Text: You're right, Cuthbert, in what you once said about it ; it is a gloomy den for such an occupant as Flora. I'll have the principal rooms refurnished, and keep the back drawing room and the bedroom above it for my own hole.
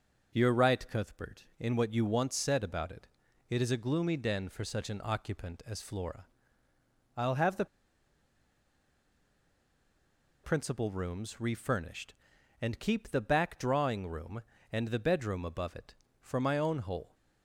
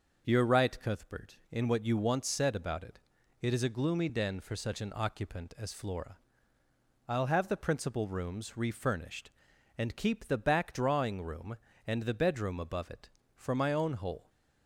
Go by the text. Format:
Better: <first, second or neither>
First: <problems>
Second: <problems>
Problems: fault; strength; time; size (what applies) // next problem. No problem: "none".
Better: second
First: pauses between "the" and "principal"; strong; at 7.6 s; 2.7 s long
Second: none